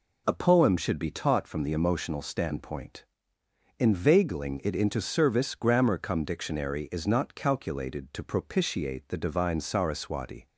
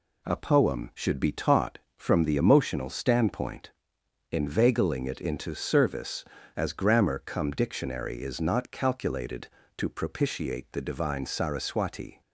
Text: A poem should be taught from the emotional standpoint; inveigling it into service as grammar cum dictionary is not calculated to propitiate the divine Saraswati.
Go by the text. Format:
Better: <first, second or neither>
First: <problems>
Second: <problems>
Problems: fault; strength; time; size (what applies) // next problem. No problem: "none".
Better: second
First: skips "as"; at 5.5 s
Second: none